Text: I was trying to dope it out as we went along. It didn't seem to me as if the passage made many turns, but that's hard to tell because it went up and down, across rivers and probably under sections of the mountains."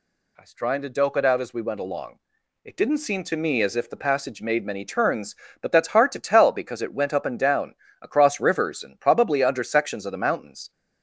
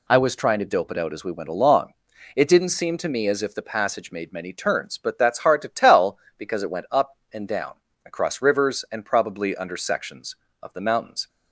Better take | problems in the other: neither | none

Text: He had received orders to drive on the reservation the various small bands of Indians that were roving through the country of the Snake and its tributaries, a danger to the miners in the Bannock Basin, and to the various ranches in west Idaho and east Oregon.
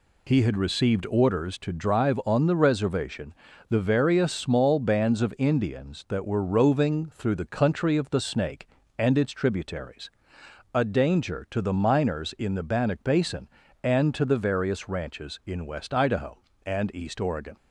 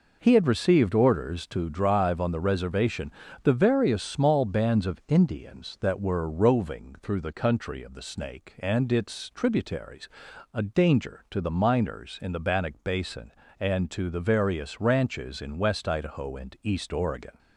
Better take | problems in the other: neither | pauses between "reservation" and "the"; slight; the same in both

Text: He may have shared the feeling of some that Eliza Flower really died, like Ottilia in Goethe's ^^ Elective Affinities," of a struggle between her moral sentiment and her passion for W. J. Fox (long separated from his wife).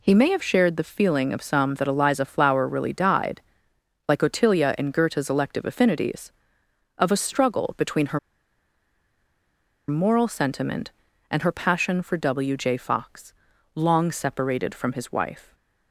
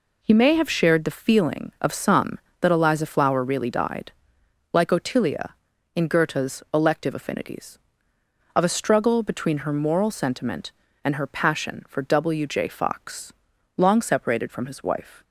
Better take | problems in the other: second | pauses between "her" and "moral"; strong; at 8.1 s; 1.6 s long

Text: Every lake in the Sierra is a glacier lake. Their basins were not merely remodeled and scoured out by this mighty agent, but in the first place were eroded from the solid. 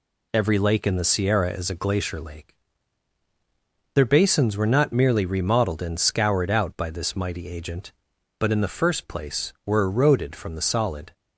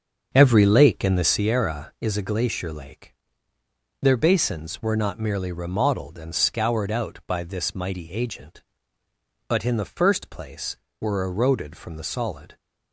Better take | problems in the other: first | starts louder than the rest; until 1.6 s; 6.5 dB

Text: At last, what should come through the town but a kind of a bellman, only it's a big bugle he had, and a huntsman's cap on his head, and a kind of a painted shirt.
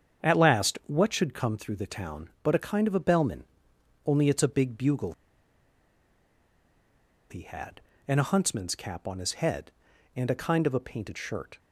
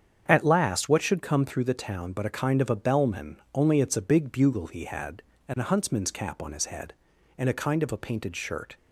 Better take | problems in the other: second | starts louder than the rest; strong; until 1.3 s; 8 dB; strong in the second // pauses between "bugle" and "he"; strong; at 5.1 s; 2.1 s long

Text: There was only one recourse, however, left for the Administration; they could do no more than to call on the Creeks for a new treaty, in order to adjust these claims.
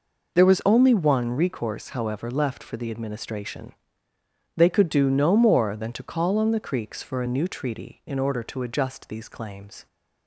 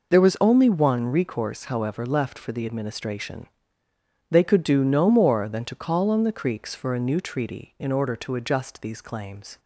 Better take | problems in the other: neither | none

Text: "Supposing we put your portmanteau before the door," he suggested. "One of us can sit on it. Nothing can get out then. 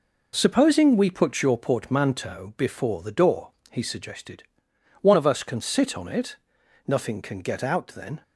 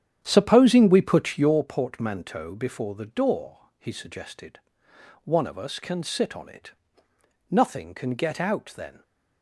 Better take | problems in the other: first | starts louder than the rest; strong; until 1.6 s; 9 dB

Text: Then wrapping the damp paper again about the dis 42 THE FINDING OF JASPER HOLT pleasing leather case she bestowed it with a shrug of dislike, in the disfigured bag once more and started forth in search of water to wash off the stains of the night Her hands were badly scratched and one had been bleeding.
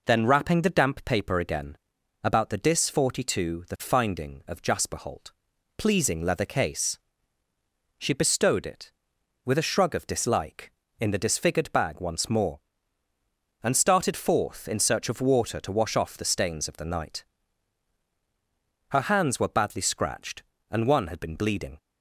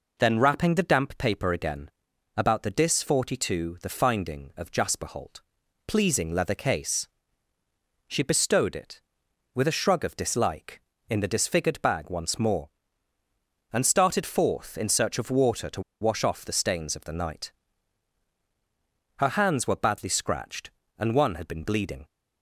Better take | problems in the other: first | pauses between "again" and "about"; noticeable; at 1.8 s; 0.48 s long; noticeable in the first // pauses between "HOLT" and "pleasing"; noticeable; at 5.4 s; 0.46 s long; noticeable in the first // pauses between "case" and "she"; at 7.0 s; 1.0 s long; also in the first // pauses between "to" and "wash"; slight; at 15.8 s; 0.20 s long // pauses between "night" and "Her"; strong; at 17.5 s; 1.6 s long; strong in the first

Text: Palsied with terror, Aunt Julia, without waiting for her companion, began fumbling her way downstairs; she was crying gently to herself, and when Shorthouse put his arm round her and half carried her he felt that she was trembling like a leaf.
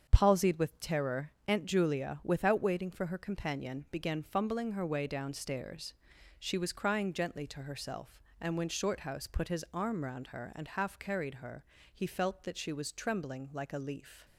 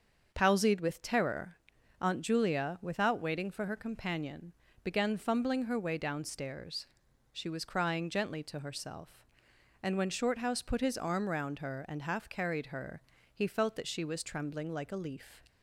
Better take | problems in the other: neither | starts louder than the rest; the same in both // pauses between "her" and "he"; slight; the same in both

